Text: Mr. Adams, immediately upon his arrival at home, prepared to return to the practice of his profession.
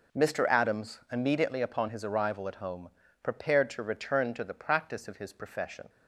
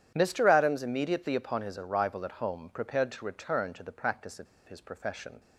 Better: first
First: none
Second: starts louder than the rest; strong; until 1.1 s; 10 dB // pauses between "of" and "his"; slight; at 4.4 s; 0.21 s long

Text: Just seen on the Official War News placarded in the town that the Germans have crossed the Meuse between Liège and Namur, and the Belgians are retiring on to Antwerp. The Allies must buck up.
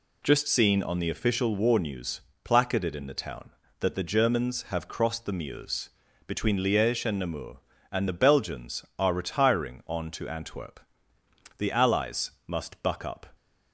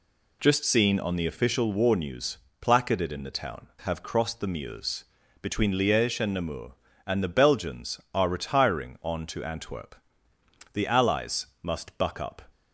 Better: first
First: pauses between "News" and "placarded"; slight; at 2.2 s; 0.24 s long // pauses between "Meuse" and "between"; at 5.8 s; 0.38 s long // pauses between "Allies" and "must"; slight; at 12.3 s; 0.16 s long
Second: pauses between "News" and "placarded"; slight; at 2.3 s; 0.24 s long // skips "that the Germans"; at 3.7 s // pauses between "Meuse" and "between"; at 5.0 s; 0.38 s long // pauses between "Allies" and "must"; slight; at 11.4 s; 0.16 s long

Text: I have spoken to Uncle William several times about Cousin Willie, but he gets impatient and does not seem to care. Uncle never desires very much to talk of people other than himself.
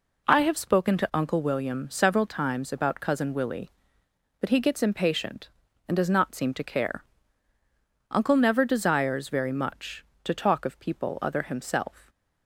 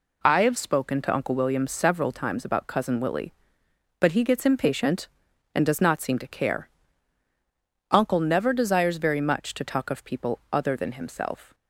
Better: second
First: skips "than"; at 11.4 s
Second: none

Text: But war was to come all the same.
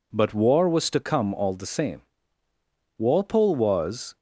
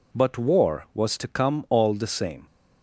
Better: second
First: goes on to say "Walpole was"; noticeable; from 2.9 s on; 1.2 s long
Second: none

